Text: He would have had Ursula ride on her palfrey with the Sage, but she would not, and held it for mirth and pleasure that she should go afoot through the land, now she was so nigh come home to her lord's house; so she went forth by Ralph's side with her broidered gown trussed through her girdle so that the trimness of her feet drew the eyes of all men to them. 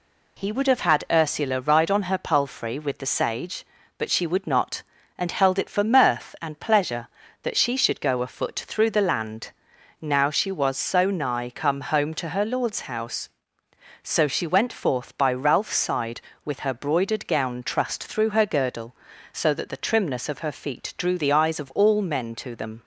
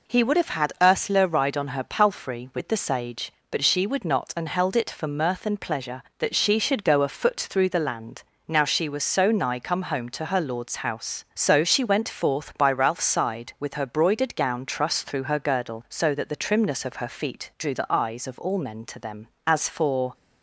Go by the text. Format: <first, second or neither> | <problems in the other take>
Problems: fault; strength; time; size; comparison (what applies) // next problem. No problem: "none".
first | goes on to say "As for"; noticeable; from 19.4 s on; 0.66 s long